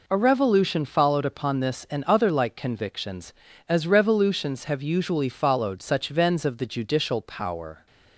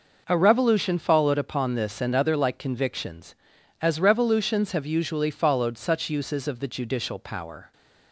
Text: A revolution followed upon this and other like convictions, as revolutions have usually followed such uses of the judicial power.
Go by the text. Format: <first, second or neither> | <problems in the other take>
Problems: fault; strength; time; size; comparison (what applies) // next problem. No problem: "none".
second | says "vens" for "uses"; at 6.0 s